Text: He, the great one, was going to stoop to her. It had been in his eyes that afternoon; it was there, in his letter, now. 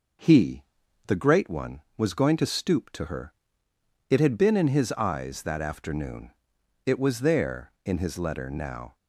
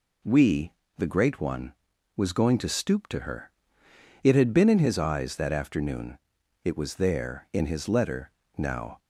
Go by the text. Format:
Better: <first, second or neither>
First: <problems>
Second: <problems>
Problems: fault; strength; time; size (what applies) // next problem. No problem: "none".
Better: first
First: none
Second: says "We" for "He"; at 0.2 s